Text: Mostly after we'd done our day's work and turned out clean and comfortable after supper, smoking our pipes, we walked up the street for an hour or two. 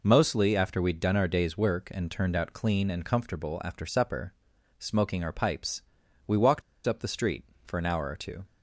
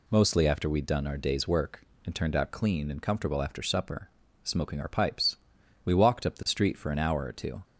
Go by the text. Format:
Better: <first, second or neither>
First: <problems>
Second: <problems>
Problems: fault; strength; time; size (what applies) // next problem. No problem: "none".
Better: second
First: pauses between "walked" and "up"; slight; at 6.6 s; 0.25 s long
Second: none